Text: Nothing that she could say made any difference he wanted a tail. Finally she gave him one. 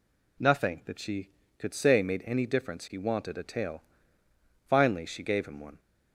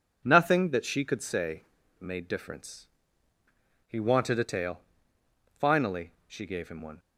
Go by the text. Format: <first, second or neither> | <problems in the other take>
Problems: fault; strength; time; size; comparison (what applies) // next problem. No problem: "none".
first | pauses between "say" and "made"; at 1.6 s; 0.38 s long // skips "any"; at 2.2 s // pauses between "difference" and "he"; at 2.8 s; 1.0 s long